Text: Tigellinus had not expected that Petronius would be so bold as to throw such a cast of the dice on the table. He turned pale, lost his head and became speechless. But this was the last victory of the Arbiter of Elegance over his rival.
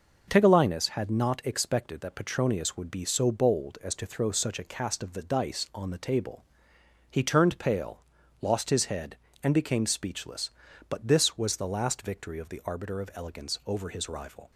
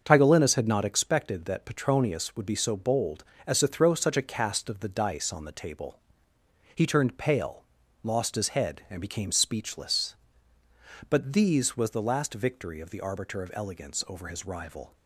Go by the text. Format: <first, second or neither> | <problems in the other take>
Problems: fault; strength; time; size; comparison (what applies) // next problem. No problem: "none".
first | starts louder than the rest; until 1.0 s; 6.5 dB // says "these" for "this"; at 11.3 s